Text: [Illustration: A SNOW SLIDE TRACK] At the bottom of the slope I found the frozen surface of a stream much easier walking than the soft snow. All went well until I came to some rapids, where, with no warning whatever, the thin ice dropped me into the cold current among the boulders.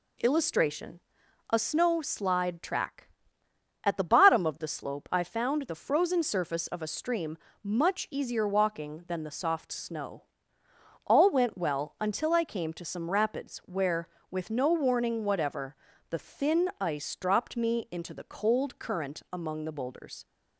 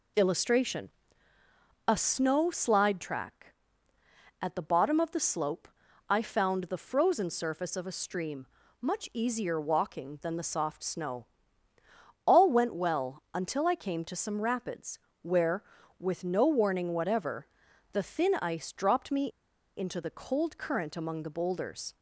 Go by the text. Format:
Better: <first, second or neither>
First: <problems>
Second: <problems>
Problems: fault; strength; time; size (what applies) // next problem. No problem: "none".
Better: first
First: pauses between "stream" and "much"; slight; at 7.3 s; 0.26 s long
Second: pauses between "slope" and "I"; at 5.6 s; 0.42 s long // pauses between "stream" and "much"; slight; at 8.4 s; 0.34 s long // pauses between "me" and "into"; noticeable; at 19.2 s; 0.48 s long